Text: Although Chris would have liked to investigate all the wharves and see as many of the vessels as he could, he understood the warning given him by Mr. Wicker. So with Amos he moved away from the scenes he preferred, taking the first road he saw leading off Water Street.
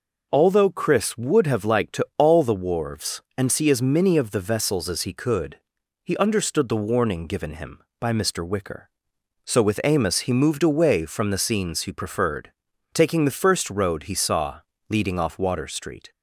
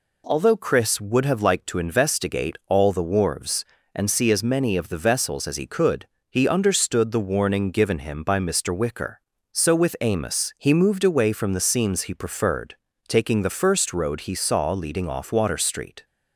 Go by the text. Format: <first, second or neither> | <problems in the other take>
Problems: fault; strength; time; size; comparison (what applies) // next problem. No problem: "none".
second | skips "investigate"; at 2.1 s // pauses between "saw" and "leading"; slight; at 14.6 s; 0.28 s long